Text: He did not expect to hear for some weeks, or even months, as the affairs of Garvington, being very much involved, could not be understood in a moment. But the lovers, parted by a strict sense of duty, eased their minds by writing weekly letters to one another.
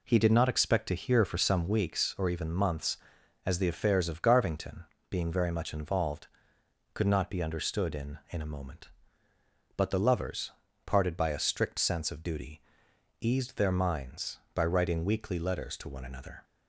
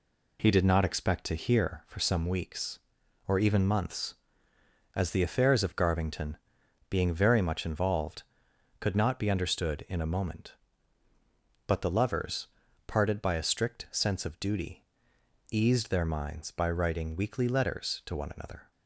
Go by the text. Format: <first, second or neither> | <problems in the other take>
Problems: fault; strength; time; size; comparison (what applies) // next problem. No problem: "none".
second | says "in" twice; at 8.2 s